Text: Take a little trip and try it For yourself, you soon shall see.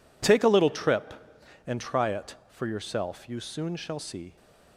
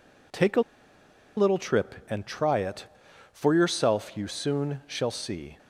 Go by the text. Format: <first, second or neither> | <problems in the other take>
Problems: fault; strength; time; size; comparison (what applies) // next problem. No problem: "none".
first | pauses between "a" and "little"; noticeable; at 0.6 s; 0.76 s long